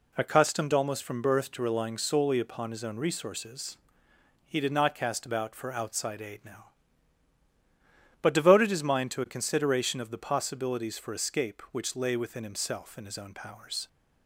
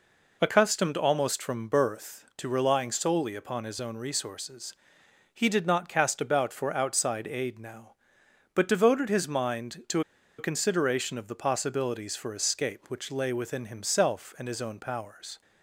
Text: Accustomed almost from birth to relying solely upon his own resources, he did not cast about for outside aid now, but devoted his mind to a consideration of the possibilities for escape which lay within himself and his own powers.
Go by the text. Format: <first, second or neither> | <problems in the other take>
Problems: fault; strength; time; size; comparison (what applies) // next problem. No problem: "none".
first | pauses between "to" and "a"; at 10.0 s; 0.37 s long